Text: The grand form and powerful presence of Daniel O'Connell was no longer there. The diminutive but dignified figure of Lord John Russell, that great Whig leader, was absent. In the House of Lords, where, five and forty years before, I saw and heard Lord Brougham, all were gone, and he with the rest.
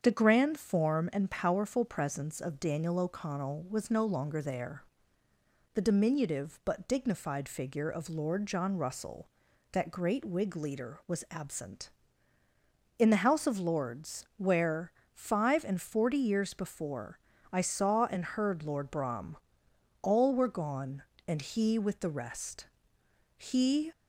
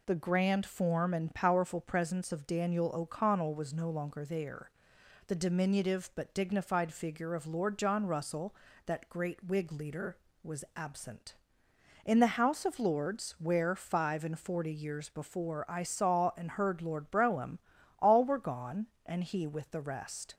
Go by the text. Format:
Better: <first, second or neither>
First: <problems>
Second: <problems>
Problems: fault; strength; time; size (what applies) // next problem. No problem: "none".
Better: second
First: starts louder than the rest; strong; until 1.0 s; 7.5 dB // goes on to say "He"; from 23.3 s on; 0.54 s long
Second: none